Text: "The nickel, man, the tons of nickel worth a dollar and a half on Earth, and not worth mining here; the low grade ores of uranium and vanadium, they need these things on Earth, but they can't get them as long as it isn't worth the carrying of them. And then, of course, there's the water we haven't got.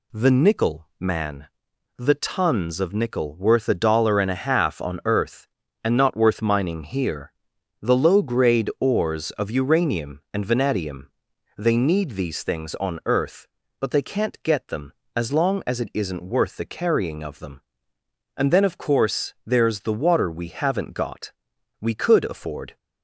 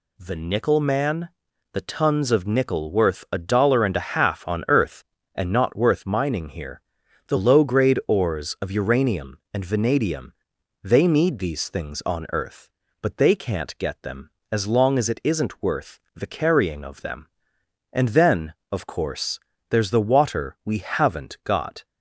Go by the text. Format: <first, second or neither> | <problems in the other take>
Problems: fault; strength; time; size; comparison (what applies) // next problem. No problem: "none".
second | goes on to say "We could afford"; noticeable; from 21.8 s on; 0.96 s long